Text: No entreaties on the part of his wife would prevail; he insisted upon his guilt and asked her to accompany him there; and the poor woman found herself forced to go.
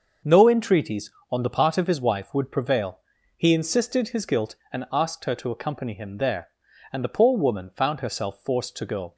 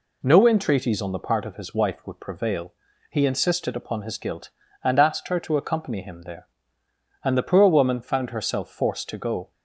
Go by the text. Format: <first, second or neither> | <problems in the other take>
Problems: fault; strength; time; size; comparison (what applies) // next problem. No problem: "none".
second | starts louder than the rest; until 1.4 s; 6.5 dB // skips "upon"; at 4.0 s